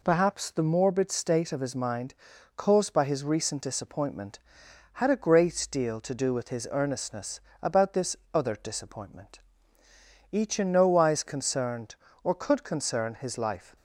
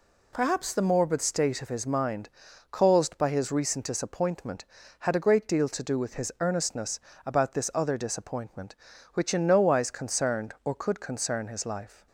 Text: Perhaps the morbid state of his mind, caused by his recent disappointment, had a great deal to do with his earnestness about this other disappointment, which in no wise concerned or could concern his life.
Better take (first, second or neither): second